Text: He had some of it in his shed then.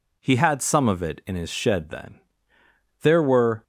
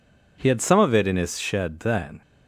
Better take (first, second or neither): second